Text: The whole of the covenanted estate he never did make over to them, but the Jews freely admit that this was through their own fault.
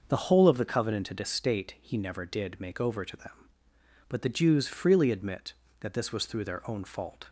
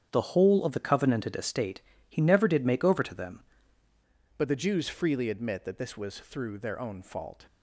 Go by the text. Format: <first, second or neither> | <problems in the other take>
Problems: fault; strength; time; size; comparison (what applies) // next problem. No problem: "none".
first | starts louder than the rest; strong; until 1.1 s; 8.5 dB; also in the first // pauses between "estate" and "he"; slight; at 1.8 s; 0.28 s long // changes voice at "but"; from 4.3 s on; 3.1 s long